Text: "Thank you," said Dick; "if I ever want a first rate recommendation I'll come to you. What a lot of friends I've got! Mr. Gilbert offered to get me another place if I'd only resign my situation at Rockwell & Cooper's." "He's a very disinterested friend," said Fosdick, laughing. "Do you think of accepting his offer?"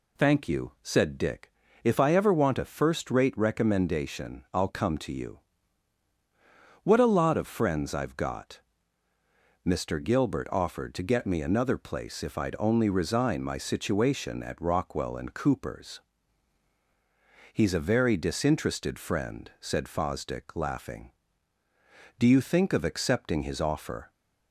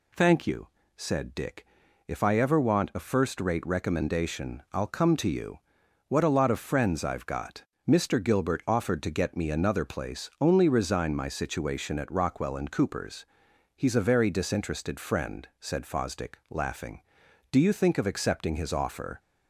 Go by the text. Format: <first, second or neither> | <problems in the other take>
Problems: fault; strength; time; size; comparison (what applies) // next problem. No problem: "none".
first | skips "if I'd"; at 10.3 s